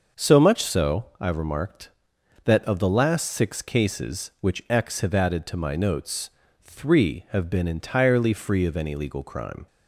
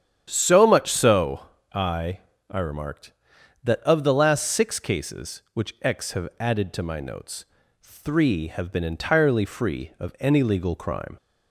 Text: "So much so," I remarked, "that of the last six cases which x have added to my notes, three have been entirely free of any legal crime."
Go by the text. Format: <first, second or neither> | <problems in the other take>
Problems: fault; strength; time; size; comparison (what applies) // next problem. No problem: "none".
first | starts louder than the rest; strong; until 1.3 s; 9.5 dB; also in the first // says "I" twice; at 2.5 s